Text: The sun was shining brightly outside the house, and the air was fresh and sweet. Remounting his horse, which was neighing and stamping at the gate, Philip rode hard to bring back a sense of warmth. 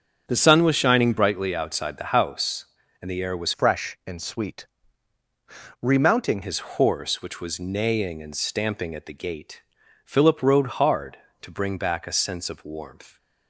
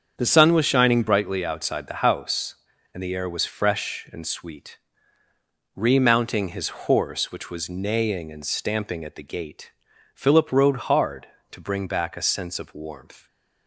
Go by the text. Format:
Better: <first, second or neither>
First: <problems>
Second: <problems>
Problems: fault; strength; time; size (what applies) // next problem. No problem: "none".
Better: second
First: starts louder than the rest; until 1.2 s; 7 dB // changes voice from "fresh" to "Remounting"; from 3.5 to 6.4 s; 2.9 s long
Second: starts louder than the rest; strong; until 1.1 s; 7.5 dB